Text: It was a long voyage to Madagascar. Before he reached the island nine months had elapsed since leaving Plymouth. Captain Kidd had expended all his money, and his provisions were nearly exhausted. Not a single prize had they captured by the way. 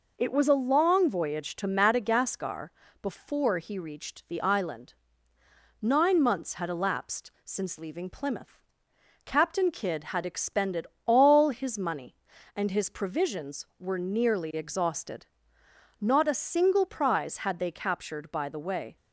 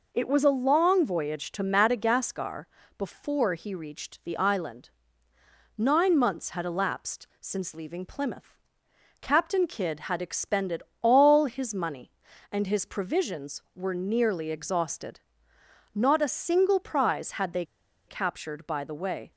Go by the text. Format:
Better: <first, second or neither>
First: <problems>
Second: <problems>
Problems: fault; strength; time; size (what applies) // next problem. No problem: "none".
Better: first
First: pauses between "island" and "nine"; noticeable; at 4.9 s; 0.88 s long // pauses between "expended" and "all"; slight; at 10.8 s; 0.18 s long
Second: pauses between "island" and "nine"; noticeable; at 4.8 s; 0.88 s long // pauses between "expended" and "all"; slight; at 10.8 s; 0.18 s long // pauses between "they" and "captured"; at 17.6 s; 0.43 s long